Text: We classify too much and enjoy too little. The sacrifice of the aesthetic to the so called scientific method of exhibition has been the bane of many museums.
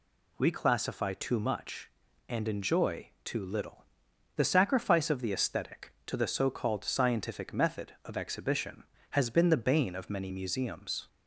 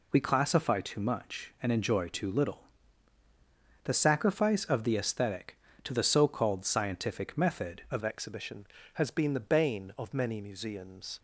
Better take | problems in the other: first | changes voice at "exhibition"; from 8.0 s on; 3.1 s long

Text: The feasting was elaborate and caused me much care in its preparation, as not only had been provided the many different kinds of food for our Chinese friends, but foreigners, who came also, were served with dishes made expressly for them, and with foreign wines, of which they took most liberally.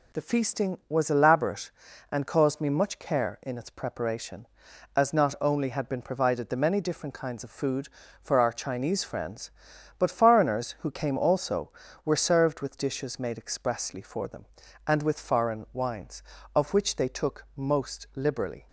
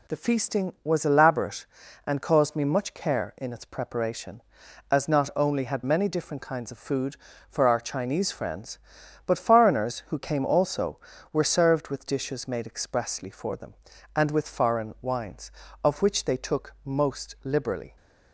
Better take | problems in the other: first | skips "been provided the"; at 5.8 s

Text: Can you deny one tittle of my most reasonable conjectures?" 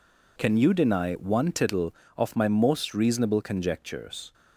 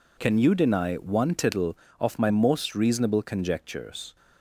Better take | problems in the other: neither | none

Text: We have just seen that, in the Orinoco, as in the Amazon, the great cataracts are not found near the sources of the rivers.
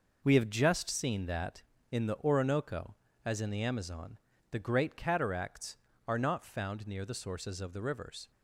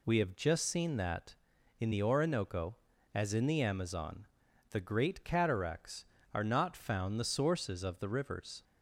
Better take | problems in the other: first | skips "near"; at 7.1 s

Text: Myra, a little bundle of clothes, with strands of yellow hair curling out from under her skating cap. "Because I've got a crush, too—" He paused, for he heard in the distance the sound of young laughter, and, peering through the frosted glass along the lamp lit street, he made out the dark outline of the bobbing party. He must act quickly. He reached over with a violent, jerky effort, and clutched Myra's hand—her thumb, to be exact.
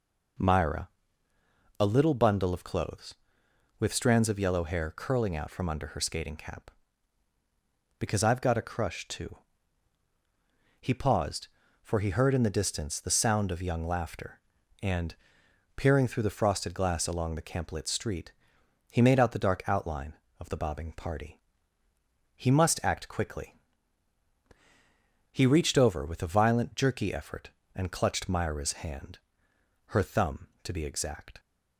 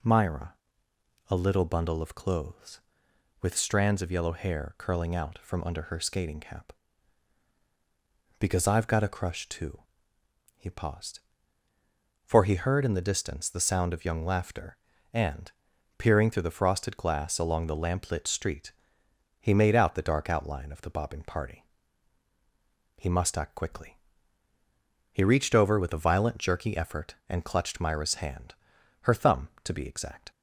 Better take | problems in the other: second | says "camp" for "lamp"; at 17.4 s

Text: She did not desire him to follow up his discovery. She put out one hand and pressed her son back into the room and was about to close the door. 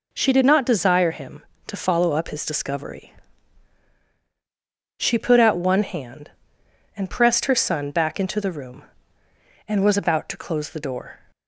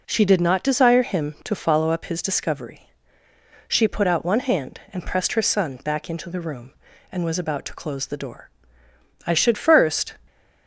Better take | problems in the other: first | goes on to say "I should first"; noticeable; from 9.2 s on; 0.90 s long

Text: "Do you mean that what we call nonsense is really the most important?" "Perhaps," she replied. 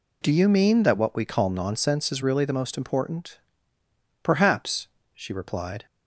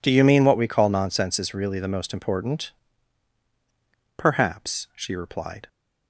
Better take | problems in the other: first | skips "that"; at 0.4 s

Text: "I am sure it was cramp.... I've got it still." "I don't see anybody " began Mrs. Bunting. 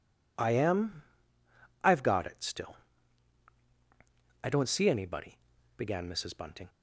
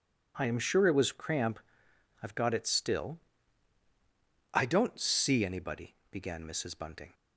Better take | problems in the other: second | skips "sure it was cramp"; at 1.4 s

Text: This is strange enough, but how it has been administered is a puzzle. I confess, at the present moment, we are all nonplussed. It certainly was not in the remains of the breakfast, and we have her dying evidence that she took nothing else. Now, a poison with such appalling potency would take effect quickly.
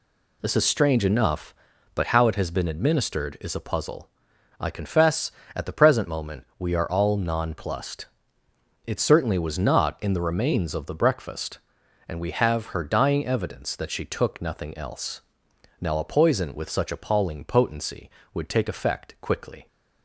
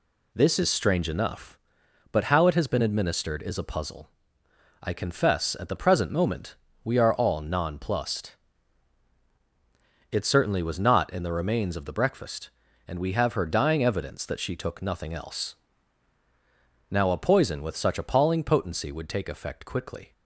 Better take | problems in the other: neither | none

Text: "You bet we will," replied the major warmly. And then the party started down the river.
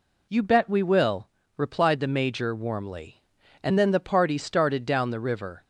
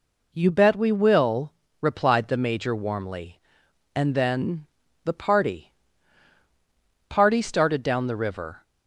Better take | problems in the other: first | pauses between "then" and "the"; at 4.6 s; 0.36 s long // says "party" twice; at 7.0 s

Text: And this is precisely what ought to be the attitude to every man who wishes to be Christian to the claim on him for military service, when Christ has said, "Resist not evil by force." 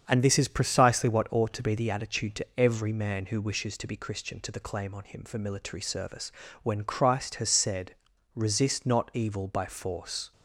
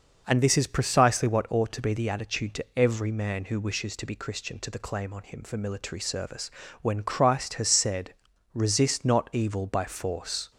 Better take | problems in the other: second | gets quieter; noticeable; throughout; 4 dB

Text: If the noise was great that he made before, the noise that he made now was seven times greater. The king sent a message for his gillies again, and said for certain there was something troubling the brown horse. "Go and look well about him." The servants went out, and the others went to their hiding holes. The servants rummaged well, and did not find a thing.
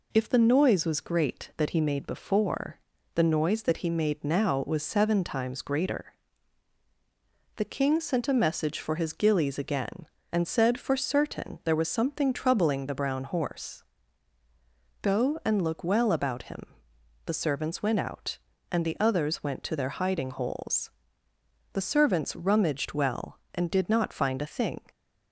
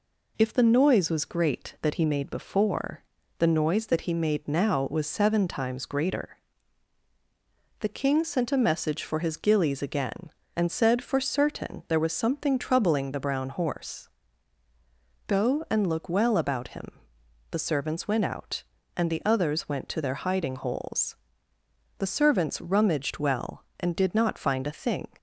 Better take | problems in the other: neither | none

